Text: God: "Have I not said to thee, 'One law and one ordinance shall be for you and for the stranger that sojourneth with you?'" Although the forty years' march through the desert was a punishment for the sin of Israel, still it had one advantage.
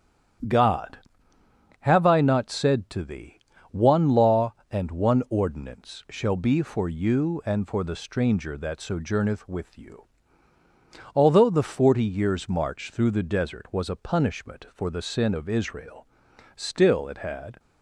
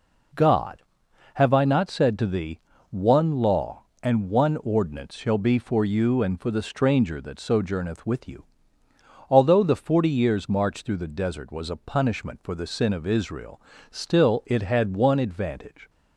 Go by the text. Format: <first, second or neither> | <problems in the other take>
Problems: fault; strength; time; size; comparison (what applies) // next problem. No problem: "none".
second | starts louder than the rest; strong; until 2.3 s; 10 dB // stops before "one advantage"; at 17.5 s